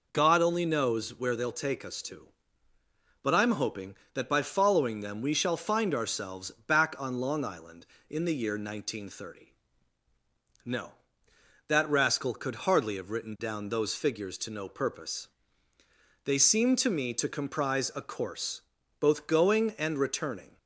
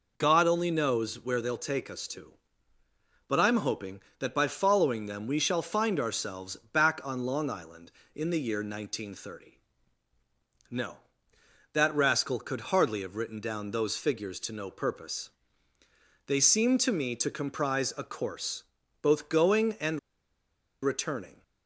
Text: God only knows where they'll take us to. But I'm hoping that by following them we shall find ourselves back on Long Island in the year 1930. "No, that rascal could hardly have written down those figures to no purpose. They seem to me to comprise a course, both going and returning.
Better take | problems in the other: first | pauses between "ourselves" and "back"; slight; at 6.5 s; 0.16 s long; slight in the first // pauses between "and" and "returning"; noticeable; at 19.9 s; 0.83 s long

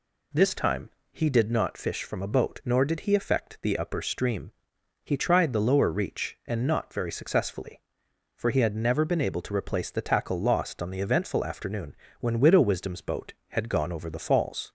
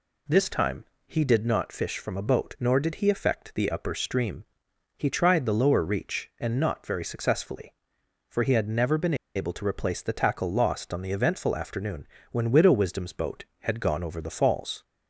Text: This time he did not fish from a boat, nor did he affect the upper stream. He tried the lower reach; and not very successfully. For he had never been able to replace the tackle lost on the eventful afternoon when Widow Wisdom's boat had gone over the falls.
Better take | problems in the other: first | pauses between "time" and "he"; slight; at 0.8 s; 0.24 s long; slight in the first // pauses between "been" and "able"; slight; at 9.1 s; 0.21 s long // pauses between "afternoon" and "when"; slight; at 12.0 s; 0.26 s long; slight in the first

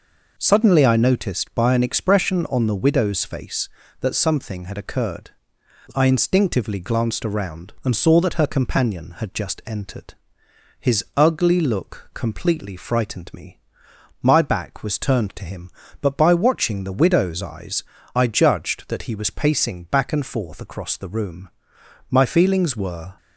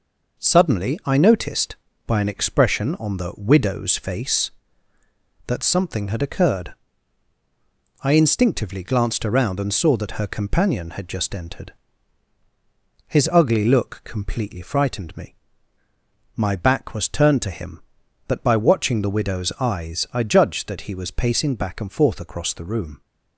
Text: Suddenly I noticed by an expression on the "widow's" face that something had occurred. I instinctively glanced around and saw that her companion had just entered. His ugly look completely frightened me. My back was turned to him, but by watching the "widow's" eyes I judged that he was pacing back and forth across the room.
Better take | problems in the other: second | pauses between "eyes" and "I"; slight; at 17.8 s; 0.32 s long // goes on to say "My feelings were"; noticeable; from 22.1 s on; 1.0 s long

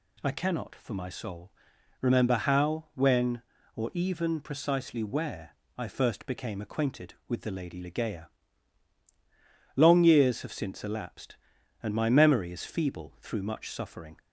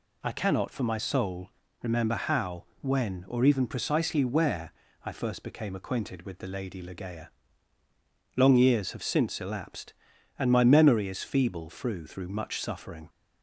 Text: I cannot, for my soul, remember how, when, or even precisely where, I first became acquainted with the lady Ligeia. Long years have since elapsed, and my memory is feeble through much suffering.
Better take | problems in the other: first | says "through" twice; at 12.0 s

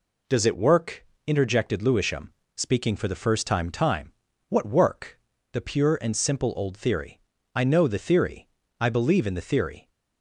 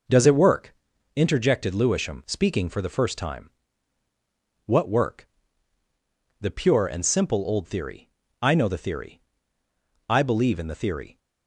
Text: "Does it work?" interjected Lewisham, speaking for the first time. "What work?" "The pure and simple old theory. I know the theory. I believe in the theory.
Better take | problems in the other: second | says "time" twice; at 3.6 s

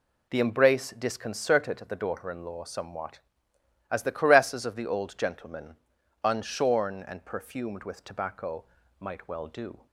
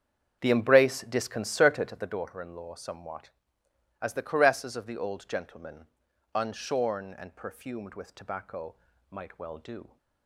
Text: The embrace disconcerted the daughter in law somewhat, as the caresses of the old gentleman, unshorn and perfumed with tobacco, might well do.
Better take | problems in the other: first | starts louder than the rest; strong; until 2.2 s; 7.5 dB

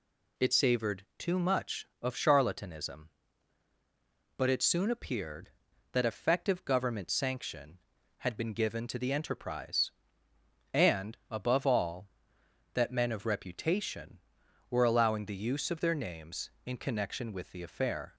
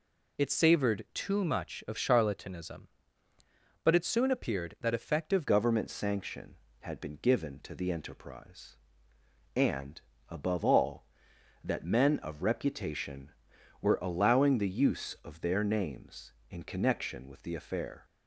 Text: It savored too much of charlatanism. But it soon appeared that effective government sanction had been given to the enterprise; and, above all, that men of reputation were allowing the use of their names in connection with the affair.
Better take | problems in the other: first | changes voice at "government"; from 5.4 s on; 12.6 s long

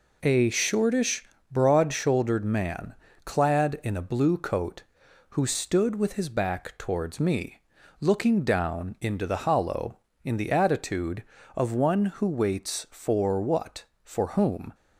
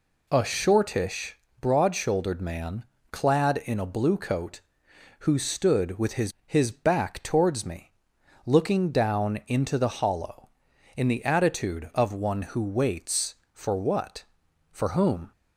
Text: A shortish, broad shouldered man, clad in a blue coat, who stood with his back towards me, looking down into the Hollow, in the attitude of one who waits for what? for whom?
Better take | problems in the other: first | says "his" twice; at 6.4 s

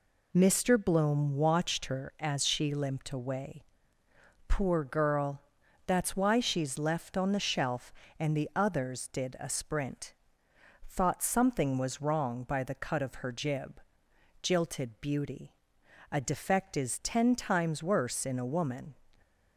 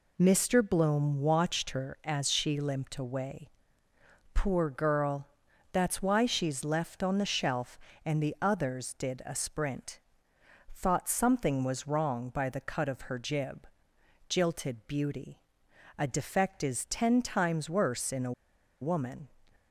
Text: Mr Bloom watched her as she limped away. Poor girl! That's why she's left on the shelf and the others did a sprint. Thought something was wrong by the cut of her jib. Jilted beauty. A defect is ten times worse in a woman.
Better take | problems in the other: first | pauses between "a" and "woman"; noticeable; at 18.3 s; 0.50 s long

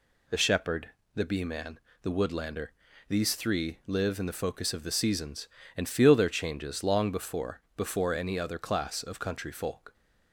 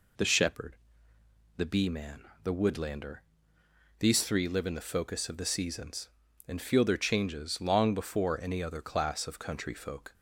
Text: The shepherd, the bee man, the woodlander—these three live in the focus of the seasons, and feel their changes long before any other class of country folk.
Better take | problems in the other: second | says "before" twice; at 7.7 s

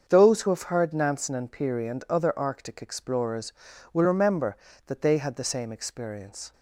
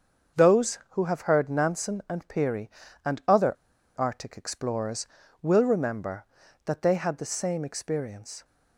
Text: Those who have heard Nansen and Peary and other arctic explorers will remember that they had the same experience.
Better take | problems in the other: first | starts louder than the rest; until 1.5 s; 6.5 dB; also in the first // pauses between "other" and "arctic"; at 3.5 s; 0.44 s long

